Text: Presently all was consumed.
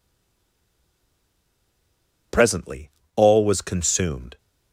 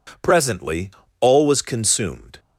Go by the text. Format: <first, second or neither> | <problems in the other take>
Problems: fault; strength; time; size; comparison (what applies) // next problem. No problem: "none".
second | stays silent before the first word; until 2.3 s; 2.3 s long // pauses between "Presently" and "all"; slight; at 2.8 s; 0.28 s long; slight in the second